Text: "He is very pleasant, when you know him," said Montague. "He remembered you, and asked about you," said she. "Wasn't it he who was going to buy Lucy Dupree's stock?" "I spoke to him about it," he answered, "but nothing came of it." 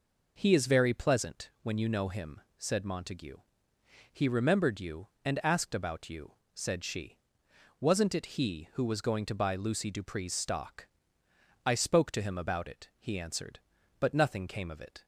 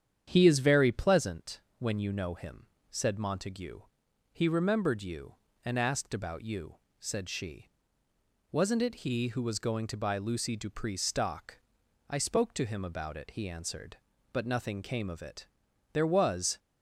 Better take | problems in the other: first | starts louder than the rest; strong; until 1.2 s; 9 dB // goes on to say "There was"; noticeable; from 15.9 s on; 0.64 s long

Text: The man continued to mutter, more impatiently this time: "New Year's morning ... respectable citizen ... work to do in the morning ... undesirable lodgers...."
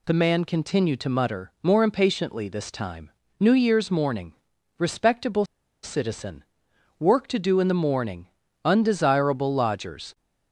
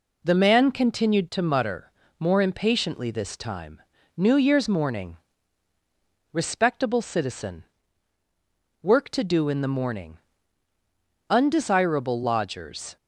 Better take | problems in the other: second | pauses between "respectable" and "citizen"; at 5.4 s; 0.37 s long

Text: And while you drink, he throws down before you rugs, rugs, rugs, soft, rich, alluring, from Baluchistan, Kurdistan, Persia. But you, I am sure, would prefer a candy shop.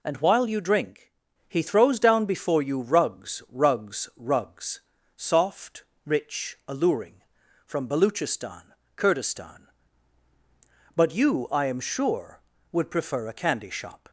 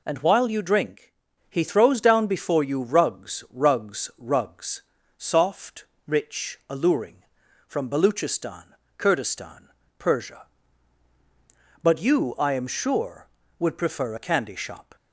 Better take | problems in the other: second | skips "Persia"; at 10.3 s

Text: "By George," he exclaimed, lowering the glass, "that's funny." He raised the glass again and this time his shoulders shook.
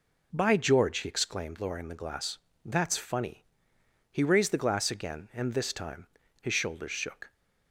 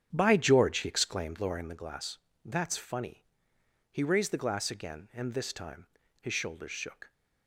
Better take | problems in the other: first | starts louder than the rest; strong; until 1.8 s; 8.5 dB // pauses between "time" and "his"; slight; at 5.8 s; 0.34 s long; slight in the first

